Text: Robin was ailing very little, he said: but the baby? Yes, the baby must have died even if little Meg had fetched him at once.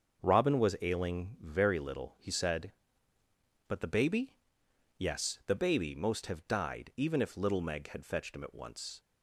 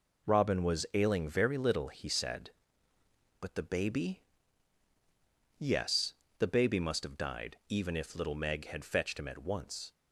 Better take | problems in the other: second | starts louder than the rest; until 1.2 s; 6.5 dB // says "most" for "must"; at 5.9 s

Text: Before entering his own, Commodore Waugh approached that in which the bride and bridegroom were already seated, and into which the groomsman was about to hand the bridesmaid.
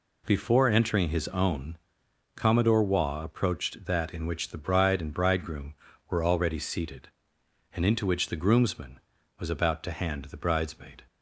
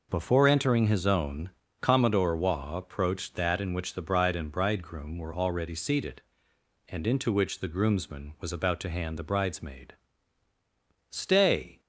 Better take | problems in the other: first | goes on to say "Stay"; noticeable; from 11.1 s on; 0.70 s long

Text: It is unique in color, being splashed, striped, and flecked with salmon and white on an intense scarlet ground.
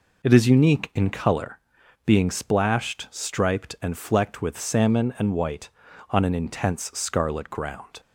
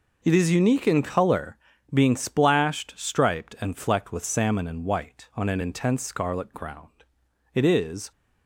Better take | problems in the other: first | goes on to say "It is"; from 7.5 s on; 0.58 s long

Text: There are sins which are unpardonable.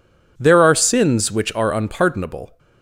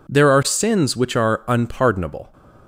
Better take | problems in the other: neither | none

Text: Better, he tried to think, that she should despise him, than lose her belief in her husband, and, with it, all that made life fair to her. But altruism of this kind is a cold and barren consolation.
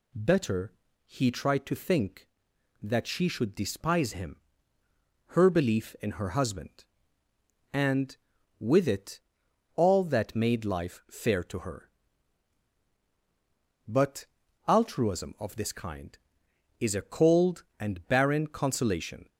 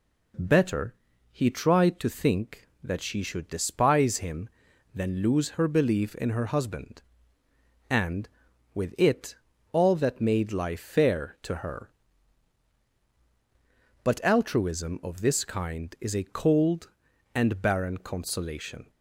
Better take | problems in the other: second | skips "than lose"; at 4.8 s // pauses between "But" and "altruism"; at 14.2 s; 0.40 s long

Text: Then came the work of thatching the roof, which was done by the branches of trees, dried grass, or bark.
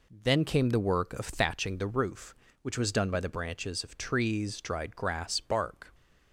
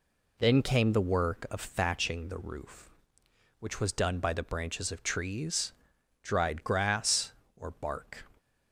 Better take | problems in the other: second | skips "or"; at 5.4 s

